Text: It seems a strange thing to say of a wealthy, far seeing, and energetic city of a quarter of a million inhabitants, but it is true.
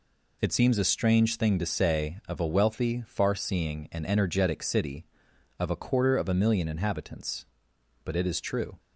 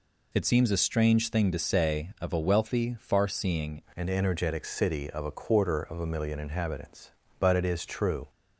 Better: first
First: none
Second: changes voice at "and"; from 3.9 s on; 4.3 s long

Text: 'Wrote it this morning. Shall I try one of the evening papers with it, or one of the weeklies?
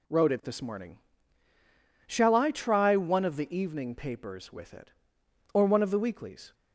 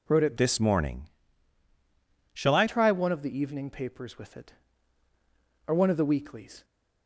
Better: first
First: none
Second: changes voice from "this" to "I"; from 0.3 to 2.6 s; 2.3 s long

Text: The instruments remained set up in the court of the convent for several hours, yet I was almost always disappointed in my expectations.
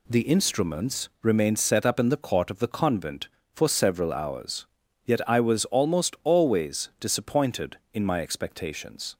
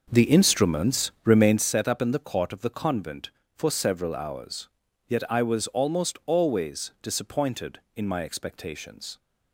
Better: first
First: none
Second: starts louder than the rest; noticeable; until 1.7 s; 5.5 dB

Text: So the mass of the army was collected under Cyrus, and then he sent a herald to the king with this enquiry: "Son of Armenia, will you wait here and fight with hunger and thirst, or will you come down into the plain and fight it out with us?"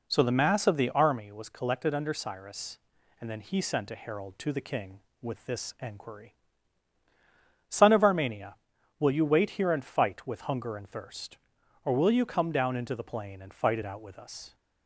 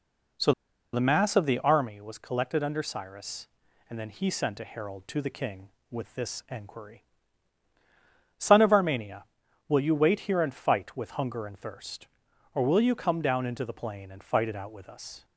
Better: first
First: none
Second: pauses between "So" and "the"; at 0.5 s; 0.41 s long

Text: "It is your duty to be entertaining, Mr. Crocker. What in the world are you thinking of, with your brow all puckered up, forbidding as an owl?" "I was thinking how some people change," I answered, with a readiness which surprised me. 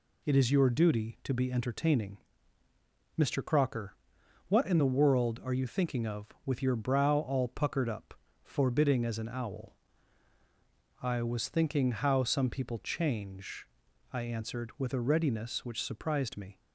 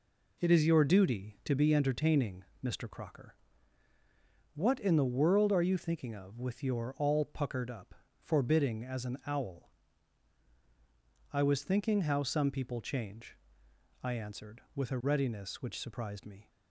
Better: first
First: none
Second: skips "brow"; at 6.9 s

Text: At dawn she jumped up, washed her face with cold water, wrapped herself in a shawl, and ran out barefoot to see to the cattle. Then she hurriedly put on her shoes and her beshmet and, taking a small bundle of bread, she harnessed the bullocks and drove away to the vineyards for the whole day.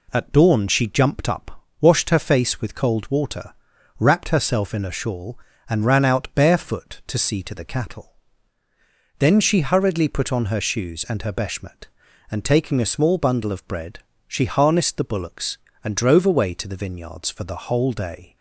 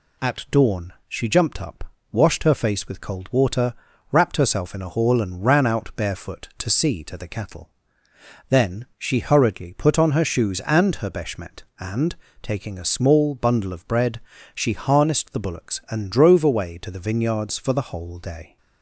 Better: first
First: none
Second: says "hall" for "shawl"; at 4.8 s

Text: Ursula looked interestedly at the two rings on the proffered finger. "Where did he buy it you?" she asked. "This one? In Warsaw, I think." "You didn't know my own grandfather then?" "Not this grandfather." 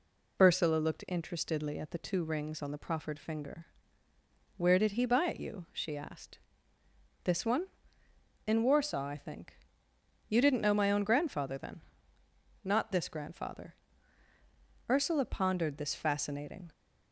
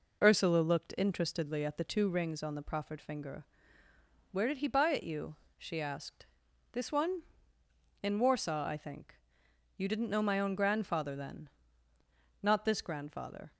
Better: second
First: goes on to say "Ursula pondered this fascinating"; strong; from 14.8 s on; 1.8 s long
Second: none

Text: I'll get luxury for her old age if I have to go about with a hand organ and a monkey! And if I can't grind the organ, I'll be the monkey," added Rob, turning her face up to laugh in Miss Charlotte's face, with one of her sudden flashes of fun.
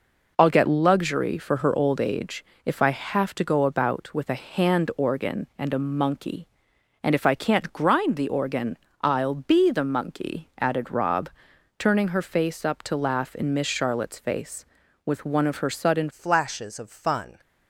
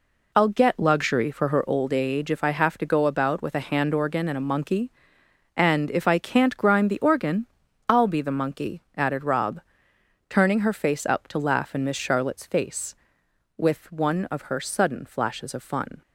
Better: second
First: pauses between "age" and "if"; slight; at 2.4 s; 0.22 s long // changes voice at "flashes"; from 16.0 s on; 1.3 s long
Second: none

